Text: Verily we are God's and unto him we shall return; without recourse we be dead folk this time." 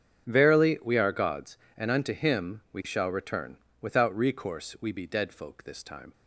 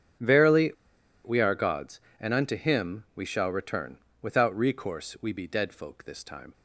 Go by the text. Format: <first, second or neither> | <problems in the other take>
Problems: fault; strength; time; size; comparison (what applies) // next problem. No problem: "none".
first | starts louder than the rest; strong; until 1.7 s; 8 dB; strong in the first // pauses between "Verily" and "we"; noticeable; at 0.7 s; 0.53 s long